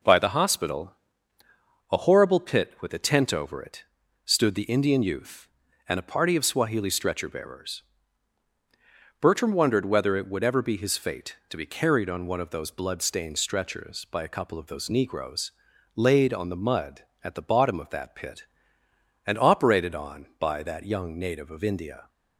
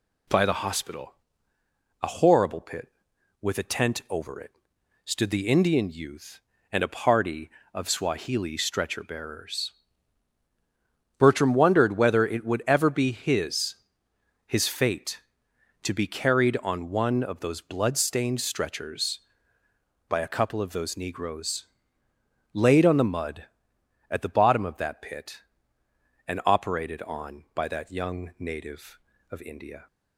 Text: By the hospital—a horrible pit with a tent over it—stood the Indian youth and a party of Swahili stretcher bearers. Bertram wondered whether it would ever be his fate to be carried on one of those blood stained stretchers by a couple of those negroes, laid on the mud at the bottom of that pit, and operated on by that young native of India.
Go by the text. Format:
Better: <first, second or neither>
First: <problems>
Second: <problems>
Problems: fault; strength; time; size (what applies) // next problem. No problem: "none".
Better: first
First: none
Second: says "his" twice; at 14.4 s